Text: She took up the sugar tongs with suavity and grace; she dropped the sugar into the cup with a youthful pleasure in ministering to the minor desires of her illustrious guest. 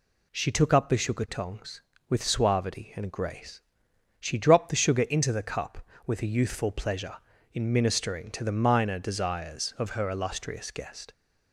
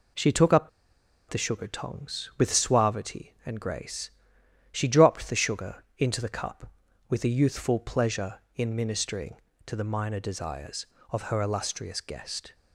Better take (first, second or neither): first